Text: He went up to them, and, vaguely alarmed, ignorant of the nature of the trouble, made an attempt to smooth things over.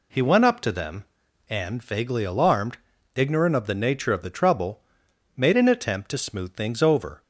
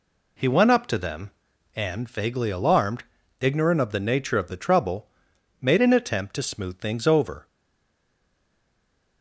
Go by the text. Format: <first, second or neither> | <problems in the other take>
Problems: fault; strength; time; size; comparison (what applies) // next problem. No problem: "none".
first | stays silent after the last word; noticeable; from 7.4 s on; 1.8 s long